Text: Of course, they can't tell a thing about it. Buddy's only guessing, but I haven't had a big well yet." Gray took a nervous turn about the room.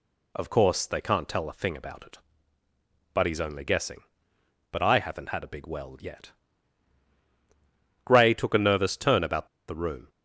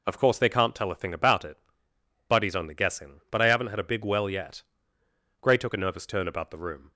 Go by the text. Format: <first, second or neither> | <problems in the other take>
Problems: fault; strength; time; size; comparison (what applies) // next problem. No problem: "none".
second | pauses between "about" and "the"; slight; at 9.4 s; 0.21 s long